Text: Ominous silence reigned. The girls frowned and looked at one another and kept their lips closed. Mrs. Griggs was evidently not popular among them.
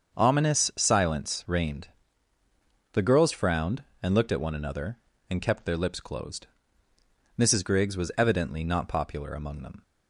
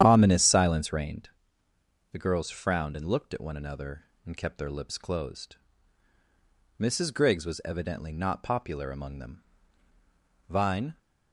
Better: first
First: starts louder than the rest; until 1.2 s; 7 dB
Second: starts louder than the rest; strong; until 1.0 s; 9.5 dB // goes on to say "Vine"; slight; from 10.4 s on; 0.48 s long

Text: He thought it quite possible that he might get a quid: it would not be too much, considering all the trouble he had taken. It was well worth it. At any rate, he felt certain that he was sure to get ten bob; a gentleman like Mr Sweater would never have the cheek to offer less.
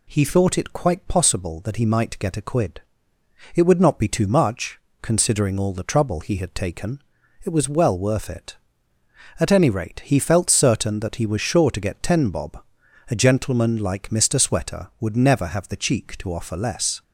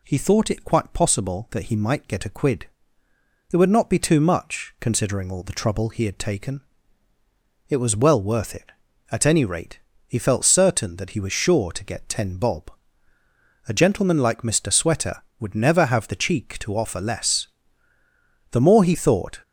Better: first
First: none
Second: goes on to say "The more he thought"; noticeable; from 18.4 s on; 0.90 s long

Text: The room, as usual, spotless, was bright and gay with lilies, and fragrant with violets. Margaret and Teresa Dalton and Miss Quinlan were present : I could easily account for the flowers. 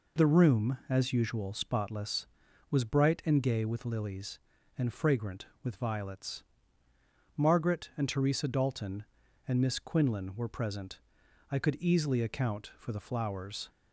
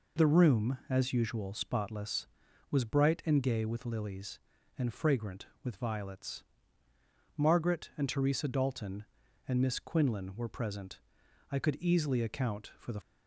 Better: first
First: none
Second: stops before "flowers"; at 13.0 s

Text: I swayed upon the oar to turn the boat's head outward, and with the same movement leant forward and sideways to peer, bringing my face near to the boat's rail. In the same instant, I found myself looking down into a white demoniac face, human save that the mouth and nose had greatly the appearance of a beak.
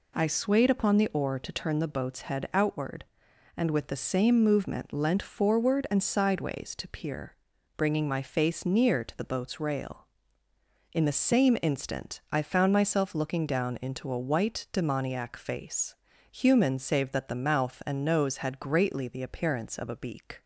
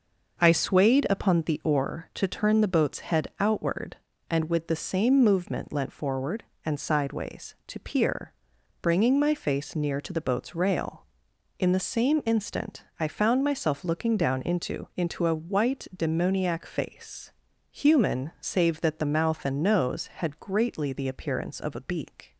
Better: first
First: none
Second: says "into" twice; at 14.9 s

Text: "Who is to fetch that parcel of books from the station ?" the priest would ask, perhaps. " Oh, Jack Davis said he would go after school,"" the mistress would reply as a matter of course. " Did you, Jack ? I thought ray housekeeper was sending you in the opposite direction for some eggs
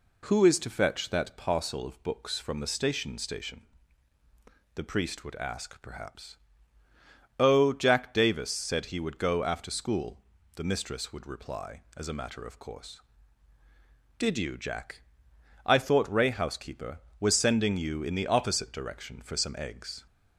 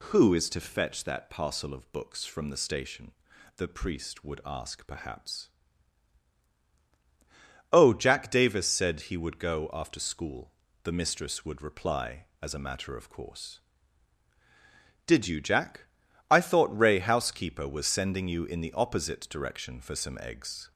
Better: second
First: says "station" twice; at 3.1 s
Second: none

